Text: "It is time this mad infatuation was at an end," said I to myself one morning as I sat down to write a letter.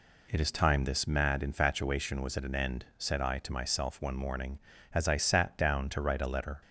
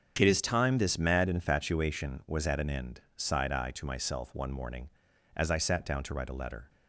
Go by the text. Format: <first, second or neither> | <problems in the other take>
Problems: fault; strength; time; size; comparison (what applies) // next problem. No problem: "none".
first | starts louder than the rest; strong; until 1.2 s; 7.5 dB // says "sighed" for "said"; at 3.1 s